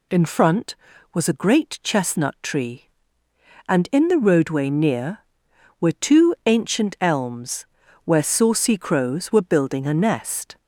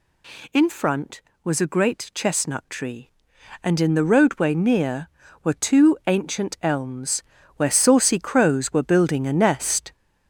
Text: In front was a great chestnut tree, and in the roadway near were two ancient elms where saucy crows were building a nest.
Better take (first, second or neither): first